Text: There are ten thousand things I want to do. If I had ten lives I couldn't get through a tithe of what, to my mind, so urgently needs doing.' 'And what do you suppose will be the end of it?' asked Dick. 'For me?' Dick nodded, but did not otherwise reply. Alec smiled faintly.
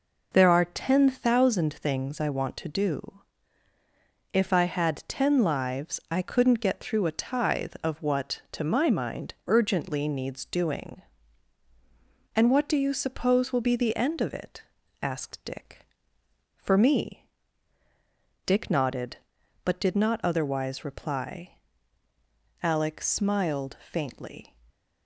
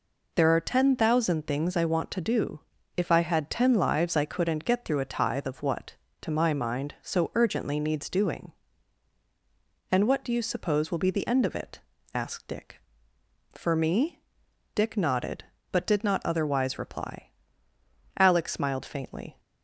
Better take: second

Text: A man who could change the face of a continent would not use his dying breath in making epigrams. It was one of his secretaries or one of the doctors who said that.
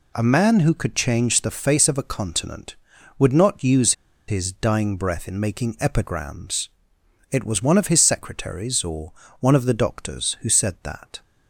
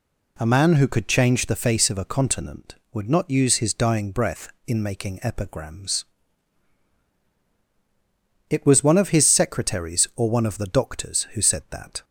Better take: second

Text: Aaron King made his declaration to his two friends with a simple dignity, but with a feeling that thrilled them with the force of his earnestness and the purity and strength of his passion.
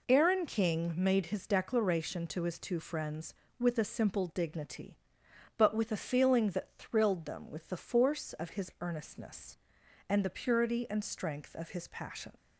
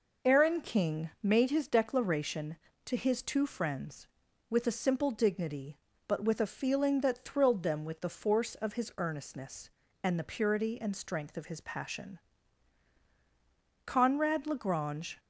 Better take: first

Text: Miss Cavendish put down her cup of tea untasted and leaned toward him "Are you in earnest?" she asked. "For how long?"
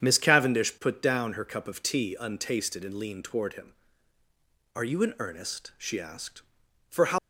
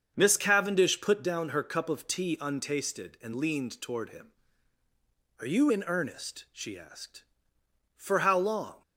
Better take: second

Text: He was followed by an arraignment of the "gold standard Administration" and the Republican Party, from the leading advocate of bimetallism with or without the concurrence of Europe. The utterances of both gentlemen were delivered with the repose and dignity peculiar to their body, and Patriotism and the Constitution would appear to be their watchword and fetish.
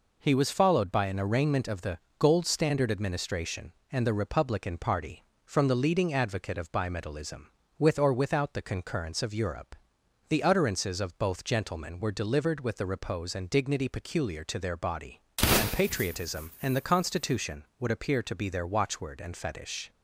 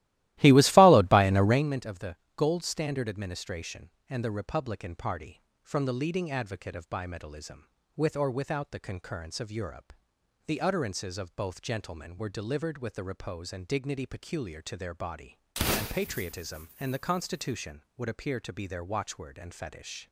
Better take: first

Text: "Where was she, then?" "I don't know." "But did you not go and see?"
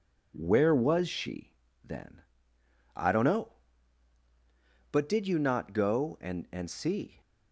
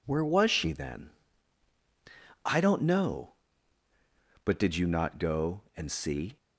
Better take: second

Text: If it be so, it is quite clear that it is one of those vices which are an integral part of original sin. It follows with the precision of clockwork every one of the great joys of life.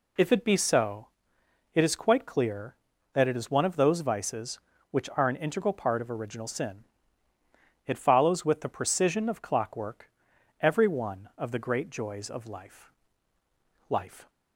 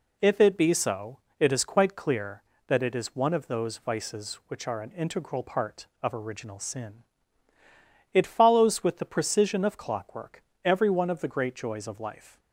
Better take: second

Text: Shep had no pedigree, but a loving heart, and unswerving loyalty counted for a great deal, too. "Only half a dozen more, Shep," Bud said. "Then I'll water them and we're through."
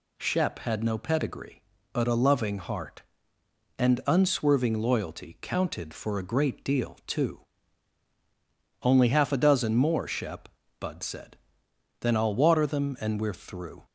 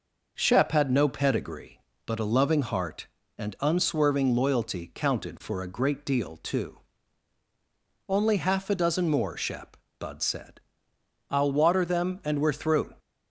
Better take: first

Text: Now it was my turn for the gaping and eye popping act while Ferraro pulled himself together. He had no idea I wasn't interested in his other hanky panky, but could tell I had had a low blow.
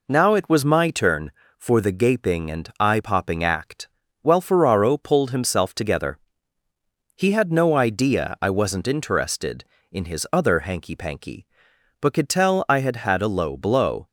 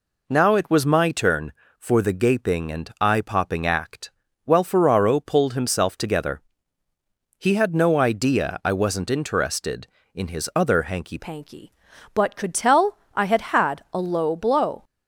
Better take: first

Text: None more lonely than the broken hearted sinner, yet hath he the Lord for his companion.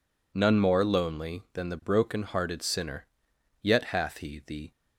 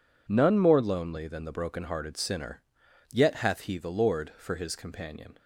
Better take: second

